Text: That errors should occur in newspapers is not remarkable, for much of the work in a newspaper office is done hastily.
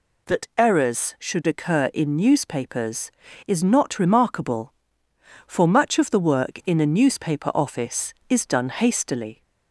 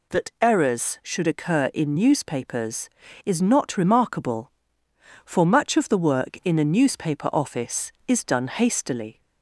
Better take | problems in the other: neither | none

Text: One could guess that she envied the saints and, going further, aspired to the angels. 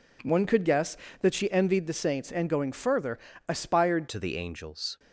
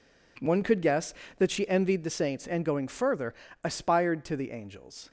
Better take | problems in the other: second | changes voice at "to"; from 4.0 s on; 0.9 s long

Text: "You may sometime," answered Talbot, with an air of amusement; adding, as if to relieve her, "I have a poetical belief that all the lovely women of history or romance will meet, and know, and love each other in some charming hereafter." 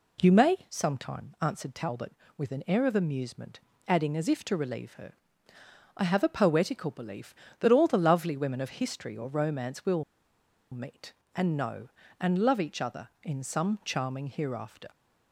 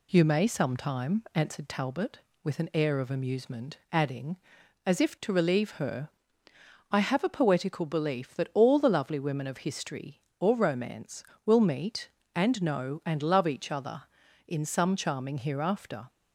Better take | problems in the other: second | pauses between "will" and "meet"; noticeable; at 10.0 s; 0.68 s long

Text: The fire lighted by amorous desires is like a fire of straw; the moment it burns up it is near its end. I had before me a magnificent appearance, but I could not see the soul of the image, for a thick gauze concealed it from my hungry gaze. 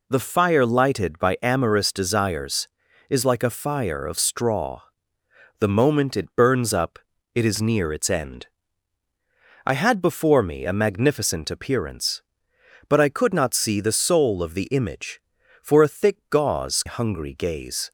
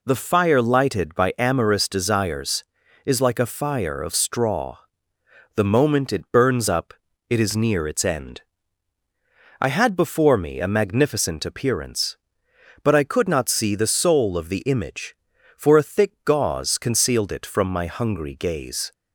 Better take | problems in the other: second | pauses between "up" and "it"; slight; at 6.9 s; 0.34 s long; slight in the second // skips "concealed it from my"; at 16.8 s

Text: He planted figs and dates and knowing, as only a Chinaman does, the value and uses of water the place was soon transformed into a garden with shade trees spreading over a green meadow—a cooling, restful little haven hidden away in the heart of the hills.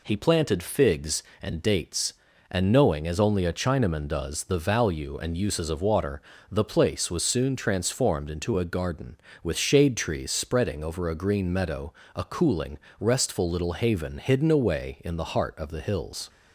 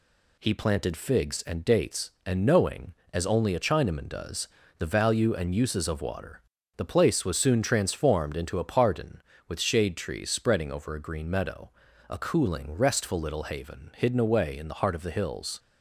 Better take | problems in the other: first | pauses between "water" and "the"; slight; at 6.4 s; 0.36 s long; slight in the first // says "pardon" for "garden"; at 8.6 s

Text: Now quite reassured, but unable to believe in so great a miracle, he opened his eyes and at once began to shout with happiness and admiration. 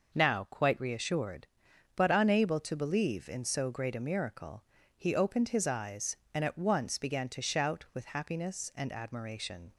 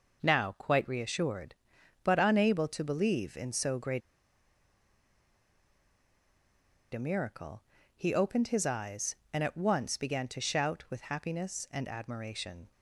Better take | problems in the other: first | pauses between "great" and "a"; strong; at 4.0 s; 2.9 s long

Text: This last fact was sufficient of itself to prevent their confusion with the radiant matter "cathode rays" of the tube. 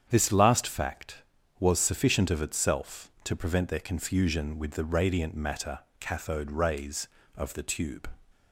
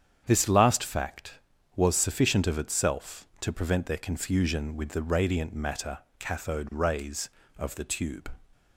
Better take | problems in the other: neither | starts louder than the rest; strong; the same in both // pauses between "matter" and "cathode"; slight; the same in both

